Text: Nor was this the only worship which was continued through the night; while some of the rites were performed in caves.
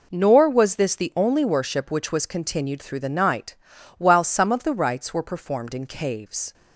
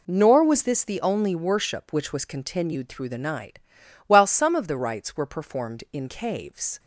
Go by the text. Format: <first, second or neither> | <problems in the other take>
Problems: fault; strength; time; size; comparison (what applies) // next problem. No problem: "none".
neither | none